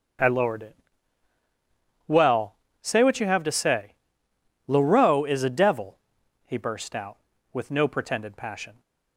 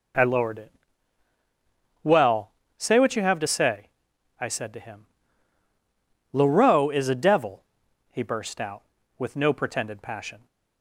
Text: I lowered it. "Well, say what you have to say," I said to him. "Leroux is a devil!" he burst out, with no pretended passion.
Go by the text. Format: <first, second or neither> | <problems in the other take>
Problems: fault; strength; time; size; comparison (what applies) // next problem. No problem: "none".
second | starts louder than the rest; until 2.5 s; 6 dB // skips "I said to him"; at 4.3 s